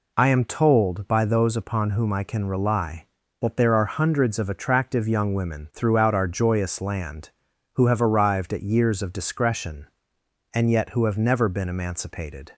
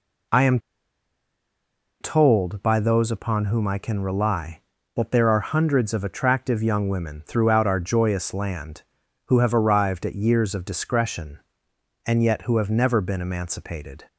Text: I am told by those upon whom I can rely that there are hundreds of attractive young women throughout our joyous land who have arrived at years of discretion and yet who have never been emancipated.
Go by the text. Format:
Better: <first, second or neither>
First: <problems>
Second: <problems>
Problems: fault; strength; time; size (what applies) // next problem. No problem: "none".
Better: first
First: none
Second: pauses between "am" and "told"; strong; at 0.5 s; 1.4 s long